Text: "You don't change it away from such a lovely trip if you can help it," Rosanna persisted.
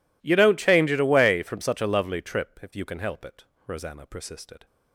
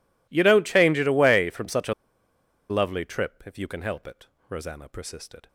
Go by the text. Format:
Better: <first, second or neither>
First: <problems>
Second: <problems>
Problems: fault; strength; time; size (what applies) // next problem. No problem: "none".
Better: first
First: none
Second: pauses between "a" and "lovely"; noticeable; at 1.9 s; 0.76 s long